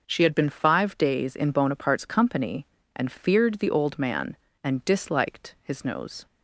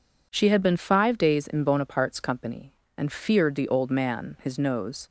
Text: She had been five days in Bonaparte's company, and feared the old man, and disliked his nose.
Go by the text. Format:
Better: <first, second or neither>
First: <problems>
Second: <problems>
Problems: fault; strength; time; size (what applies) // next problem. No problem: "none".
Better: first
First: none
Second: skips "and disliked"; at 4.3 s